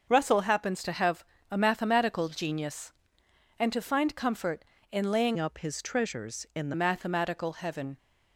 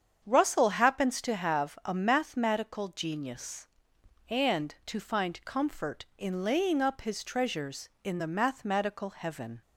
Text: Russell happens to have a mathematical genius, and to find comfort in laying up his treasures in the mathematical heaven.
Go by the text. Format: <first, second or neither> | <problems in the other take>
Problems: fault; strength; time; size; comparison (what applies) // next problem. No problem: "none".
second | starts louder than the rest; until 1.1 s; 6.5 dB; strong in the second // pauses between "have" and "a"; slight; at 1.2 s; 0.26 s long // changes voice from "up" to "the"; from 5.3 to 6.7 s; 1.4 s long